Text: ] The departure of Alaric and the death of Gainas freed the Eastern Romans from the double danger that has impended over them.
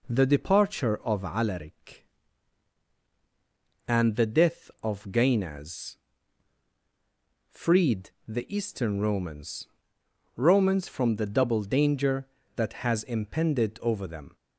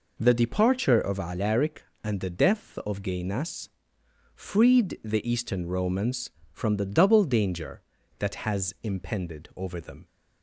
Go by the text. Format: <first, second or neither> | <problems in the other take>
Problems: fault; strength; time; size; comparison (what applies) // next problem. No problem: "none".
second | pauses between "Gainas" and "freed"; strong; at 5.9 s; 1.5 s long; noticeable in the second // pauses between "freed" and "the"; slight; at 8.0 s; 0.18 s long // says "Romans" twice; at 10.3 s